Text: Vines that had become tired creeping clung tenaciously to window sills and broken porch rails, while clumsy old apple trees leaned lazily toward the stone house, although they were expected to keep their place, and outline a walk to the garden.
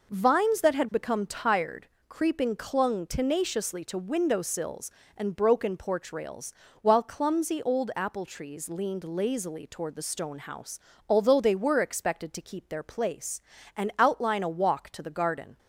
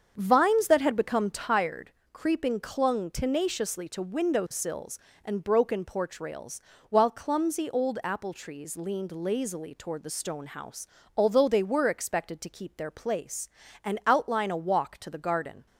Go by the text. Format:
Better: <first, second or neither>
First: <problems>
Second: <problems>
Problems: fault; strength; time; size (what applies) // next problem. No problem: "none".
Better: first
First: pauses between "tired" and "creeping"; slight; at 1.8 s; 0.22 s long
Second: starts louder than the rest; strong; until 1.6 s; 7 dB // pauses between "tired" and "creeping"; slight; at 1.8 s; 0.22 s long